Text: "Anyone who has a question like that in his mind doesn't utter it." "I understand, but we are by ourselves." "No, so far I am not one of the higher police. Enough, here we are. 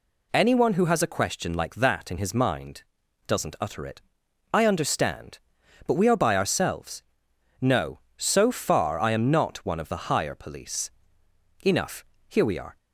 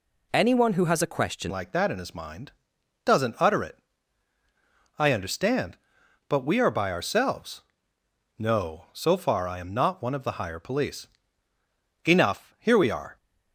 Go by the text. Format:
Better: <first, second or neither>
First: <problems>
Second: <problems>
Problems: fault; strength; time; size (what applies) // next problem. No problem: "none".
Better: first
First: pauses between "mind" and "doesn't"; at 2.8 s; 0.44 s long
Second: changes voice at "like"; from 1.4 s on; 11.7 s long // pauses between "mind" and "doesn't"; noticeable; at 2.5 s; 0.52 s long